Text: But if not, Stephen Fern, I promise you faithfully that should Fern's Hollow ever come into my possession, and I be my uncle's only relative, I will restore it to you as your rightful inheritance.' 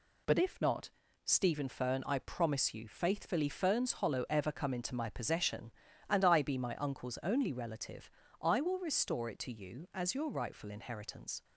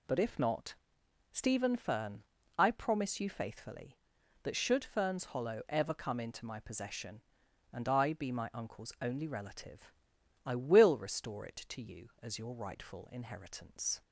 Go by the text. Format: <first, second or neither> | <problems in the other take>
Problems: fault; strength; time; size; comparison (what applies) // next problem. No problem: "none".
second | skips "that should"; at 3.4 s